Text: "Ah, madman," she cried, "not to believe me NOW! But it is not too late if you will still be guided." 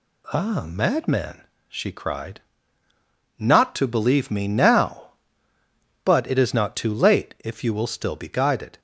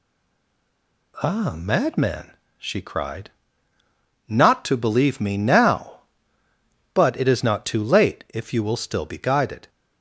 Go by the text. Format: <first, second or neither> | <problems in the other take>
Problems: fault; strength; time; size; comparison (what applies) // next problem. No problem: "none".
first | stays silent before the first word; until 1.1 s; 1.1 s long